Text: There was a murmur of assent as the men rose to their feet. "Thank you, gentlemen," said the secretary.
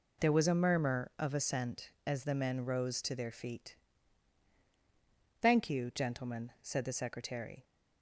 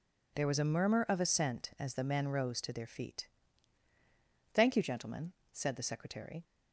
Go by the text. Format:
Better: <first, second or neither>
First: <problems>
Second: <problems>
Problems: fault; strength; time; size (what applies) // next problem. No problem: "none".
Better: neither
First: none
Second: none